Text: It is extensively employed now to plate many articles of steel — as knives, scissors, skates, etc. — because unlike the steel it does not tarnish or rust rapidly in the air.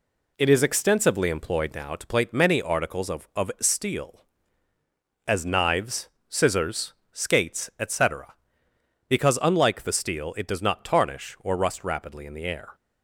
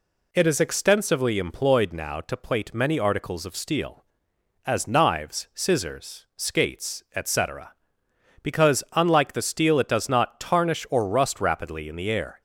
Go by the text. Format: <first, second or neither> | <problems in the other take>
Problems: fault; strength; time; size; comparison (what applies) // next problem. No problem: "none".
second | says "of" twice; at 3.3 s